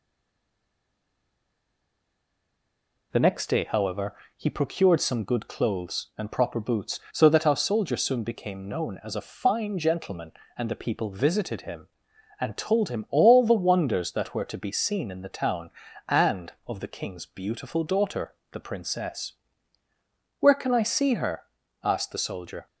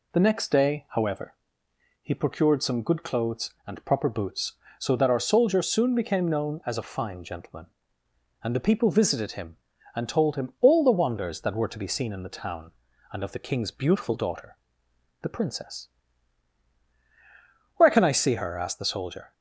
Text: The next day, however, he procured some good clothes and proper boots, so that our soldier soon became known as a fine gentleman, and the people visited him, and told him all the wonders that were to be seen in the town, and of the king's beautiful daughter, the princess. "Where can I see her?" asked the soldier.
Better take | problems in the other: second | stays silent before the first word; strong; until 3.1 s; 3.1 s long

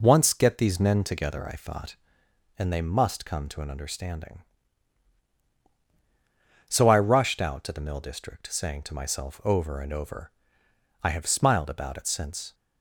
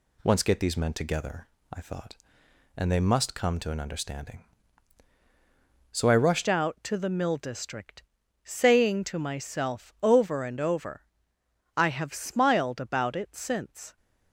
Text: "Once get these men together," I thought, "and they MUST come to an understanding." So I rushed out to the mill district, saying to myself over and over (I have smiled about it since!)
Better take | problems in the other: first | changes voice at "out"; from 6.4 s on; 7.5 s long

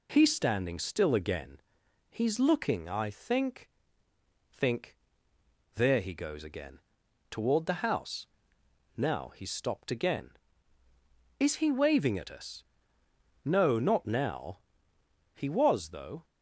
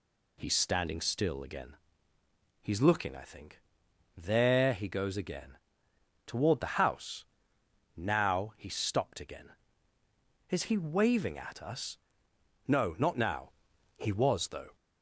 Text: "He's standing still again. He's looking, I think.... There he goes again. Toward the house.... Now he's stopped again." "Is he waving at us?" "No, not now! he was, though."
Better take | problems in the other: second | says "think" twice; at 4.5 s

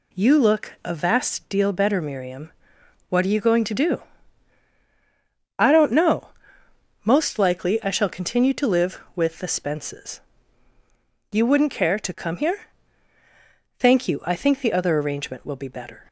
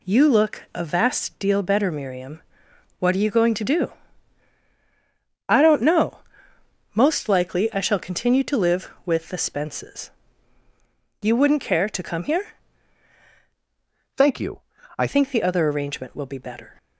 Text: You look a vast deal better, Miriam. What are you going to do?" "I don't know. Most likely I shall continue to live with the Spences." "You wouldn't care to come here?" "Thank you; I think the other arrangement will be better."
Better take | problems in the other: first | changes voice from "Thank" to "I"; from 14.1 to 15.0 s; 0.9 s long

